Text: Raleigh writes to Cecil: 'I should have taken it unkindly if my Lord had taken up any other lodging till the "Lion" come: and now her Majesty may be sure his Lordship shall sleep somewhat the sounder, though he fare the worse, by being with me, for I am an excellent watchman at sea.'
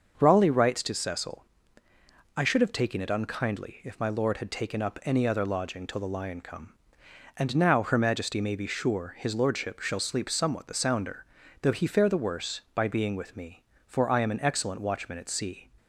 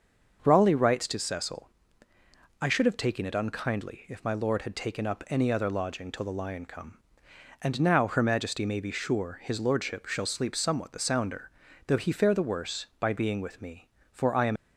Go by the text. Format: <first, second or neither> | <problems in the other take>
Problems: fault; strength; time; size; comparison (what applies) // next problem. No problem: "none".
first | starts louder than the rest; until 1.4 s; 6.5 dB; also in the first // stops before "an excellent watchman at sea"; at 14.5 s